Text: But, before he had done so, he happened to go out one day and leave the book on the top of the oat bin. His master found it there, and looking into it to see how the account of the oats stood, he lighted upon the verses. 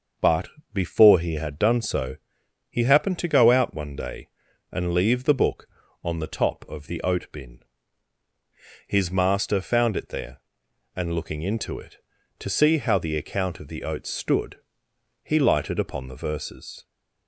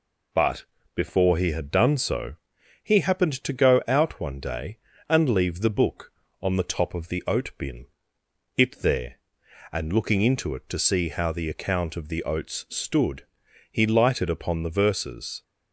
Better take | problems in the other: first | skips "His master found"; at 8.2 s

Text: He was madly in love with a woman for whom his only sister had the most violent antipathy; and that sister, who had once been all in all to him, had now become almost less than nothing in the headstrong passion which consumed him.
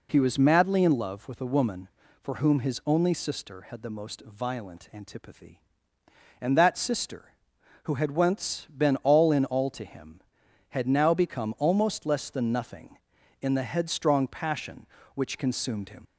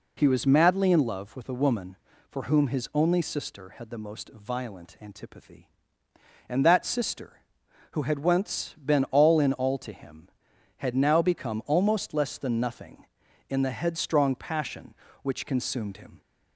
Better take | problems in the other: second | leaves "him" unfinished; at 16.0 s; 70 ms

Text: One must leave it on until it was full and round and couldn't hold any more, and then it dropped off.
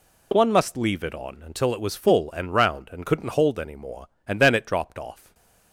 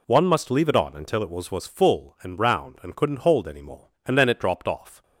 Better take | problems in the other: first | says "was" twice; at 1.5 s

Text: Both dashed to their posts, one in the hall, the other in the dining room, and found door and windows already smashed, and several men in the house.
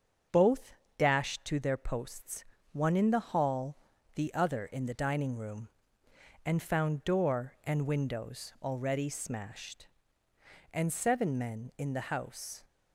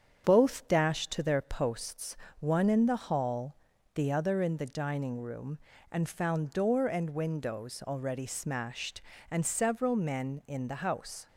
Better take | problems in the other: second | starts louder than the rest; strong; until 1.5 s; 7.5 dB; strong in the second // pauses between "Both" and "dashed"; slight; at 0.7 s; 0.24 s long // says "seven" for "several"; at 10.9 s

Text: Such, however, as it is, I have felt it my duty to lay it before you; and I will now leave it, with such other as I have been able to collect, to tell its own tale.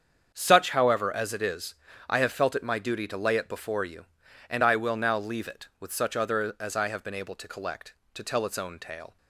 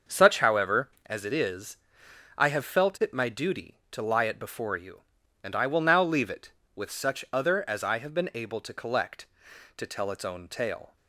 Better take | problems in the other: first | starts louder than the rest; until 1.2 s; 6.5 dB; strong in the first // says "lie" for "lay"; at 4.0 s

